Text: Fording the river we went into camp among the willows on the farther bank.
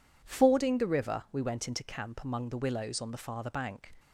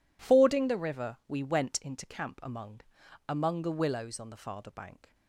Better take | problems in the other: first | says "among" twice; at 3.2 s

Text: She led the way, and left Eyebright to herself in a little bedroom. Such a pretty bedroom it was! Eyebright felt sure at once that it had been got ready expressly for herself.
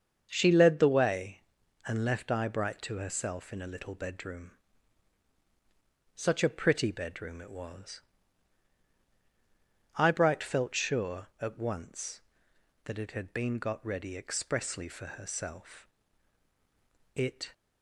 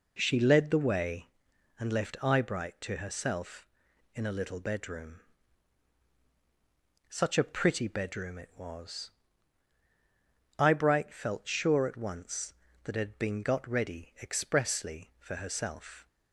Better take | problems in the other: second | starts louder than the rest; until 1.3 s; 7 dB // goes on to say "It"; slight; from 17.1 s on; 0.38 s long

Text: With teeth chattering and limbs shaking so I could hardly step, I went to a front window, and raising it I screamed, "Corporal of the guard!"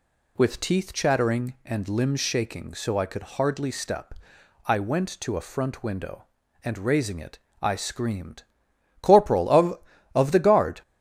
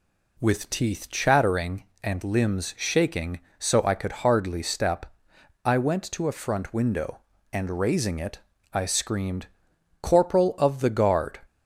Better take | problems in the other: second | pauses between "it" and "I"; slight; at 7.3 s; 0.24 s long; slight in the second // says "of" twice; at 10.1 s

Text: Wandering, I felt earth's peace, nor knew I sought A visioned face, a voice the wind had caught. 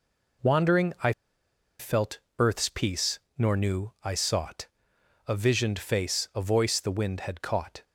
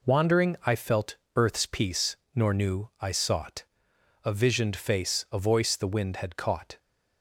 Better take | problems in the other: second | pauses between "I" and "felt"; noticeable; at 1.1 s; 0.68 s long // pauses between "felt" and "earth's"; slight; at 2.1 s; 0.20 s long; slight in the second // pauses between "sought" and "A"; noticeable; at 4.6 s; 0.62 s long; noticeable in the second

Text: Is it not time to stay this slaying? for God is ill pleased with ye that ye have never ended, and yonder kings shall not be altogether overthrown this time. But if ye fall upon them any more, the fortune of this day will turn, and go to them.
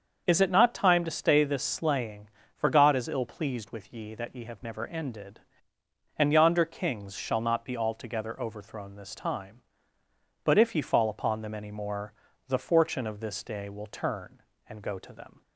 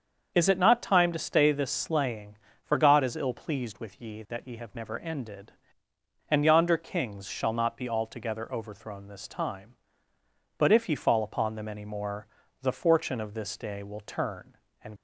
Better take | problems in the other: first | starts louder than the rest; until 1.3 s; 6.5 dB; also in the first // stops before "go to them"; at 14.9 s

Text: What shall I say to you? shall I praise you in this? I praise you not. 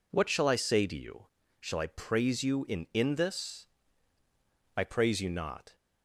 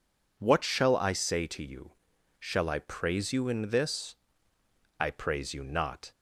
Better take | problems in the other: second | says "in" twice; at 2.9 s

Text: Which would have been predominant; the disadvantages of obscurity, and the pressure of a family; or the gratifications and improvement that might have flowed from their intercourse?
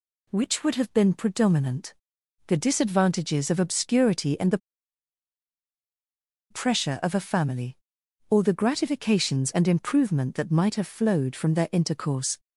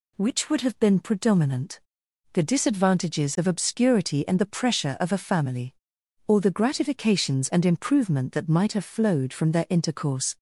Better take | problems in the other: second | pauses between "the" and "pressure"; strong; at 4.5 s; 1.9 s long

